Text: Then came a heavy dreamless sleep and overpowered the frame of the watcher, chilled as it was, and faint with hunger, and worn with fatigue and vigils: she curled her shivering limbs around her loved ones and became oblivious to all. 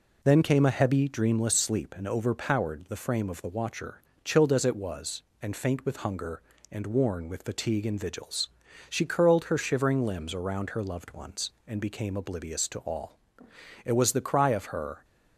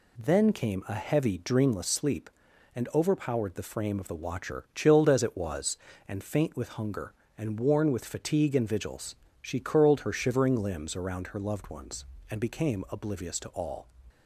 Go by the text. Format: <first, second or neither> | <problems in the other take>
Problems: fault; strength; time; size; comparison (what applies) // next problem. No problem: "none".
second | goes on to say "It was the cry of her"; noticeable; from 13.8 s on; 1.2 s long